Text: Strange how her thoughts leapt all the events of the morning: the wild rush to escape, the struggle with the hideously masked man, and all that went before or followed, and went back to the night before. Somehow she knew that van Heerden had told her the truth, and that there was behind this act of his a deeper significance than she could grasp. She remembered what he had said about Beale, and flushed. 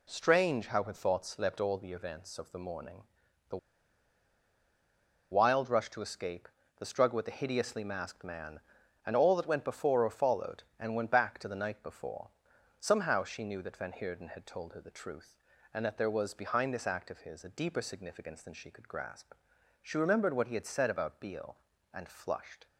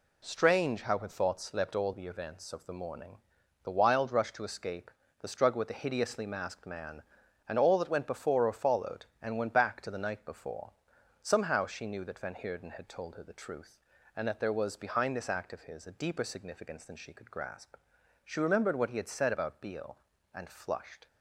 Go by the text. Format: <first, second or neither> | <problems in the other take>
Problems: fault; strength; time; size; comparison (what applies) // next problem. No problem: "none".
second | pauses between "the" and "wild"; strong; at 3.5 s; 1.7 s long